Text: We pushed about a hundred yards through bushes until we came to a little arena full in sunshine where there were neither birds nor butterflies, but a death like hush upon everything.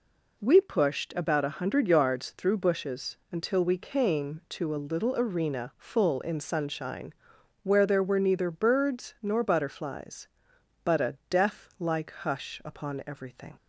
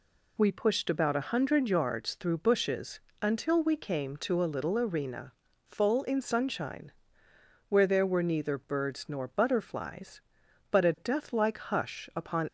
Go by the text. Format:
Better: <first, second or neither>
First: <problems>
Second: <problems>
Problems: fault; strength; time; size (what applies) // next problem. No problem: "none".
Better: first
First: pauses between "sunshine" and "where"; noticeable; at 7.1 s; 0.50 s long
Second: pauses between "bushes" and "until"; slight; at 2.9 s; 0.24 s long // pauses between "arena" and "full"; slight; at 5.3 s; 0.34 s long // pauses between "sunshine" and "where"; noticeable; at 6.9 s; 0.78 s long // stops before "everything"; at 12.4 s